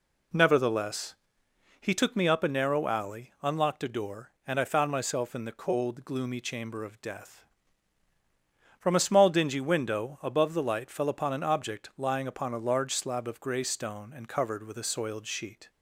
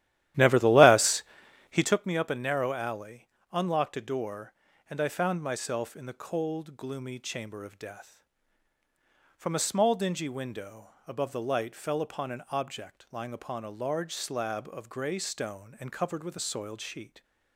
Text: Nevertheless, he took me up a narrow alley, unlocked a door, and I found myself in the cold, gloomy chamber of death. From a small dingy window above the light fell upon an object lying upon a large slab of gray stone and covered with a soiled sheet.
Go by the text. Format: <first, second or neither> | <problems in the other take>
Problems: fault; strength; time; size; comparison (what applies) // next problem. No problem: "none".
first | starts louder than the rest; strong; until 2.1 s; 13 dB // pauses between "window" and "above"; slight; at 10.9 s; 0.16 s long